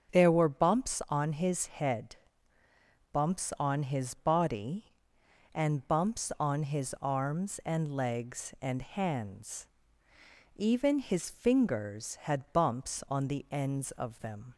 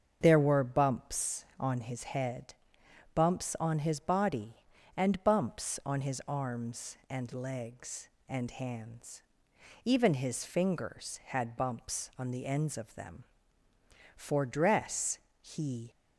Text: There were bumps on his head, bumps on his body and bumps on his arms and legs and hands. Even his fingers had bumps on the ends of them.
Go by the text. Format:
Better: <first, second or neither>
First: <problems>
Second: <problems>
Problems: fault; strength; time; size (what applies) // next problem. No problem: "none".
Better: first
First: starts louder than the rest; until 1.2 s; 7 dB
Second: starts louder than the rest; until 1.2 s; 7 dB // goes on to say "For dress he"; strong; from 14.1 s on; 1.7 s long